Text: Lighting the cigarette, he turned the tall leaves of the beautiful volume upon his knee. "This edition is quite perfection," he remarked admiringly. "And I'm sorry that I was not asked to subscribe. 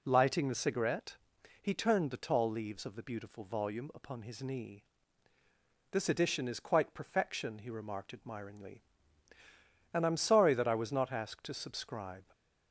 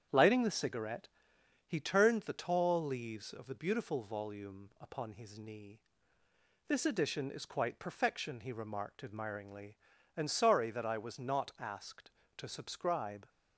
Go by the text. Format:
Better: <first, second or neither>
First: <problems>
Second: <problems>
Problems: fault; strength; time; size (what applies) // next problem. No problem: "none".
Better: first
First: none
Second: starts louder than the rest; strong; until 1.6 s; 8.5 dB // skips "I'm"; at 10.2 s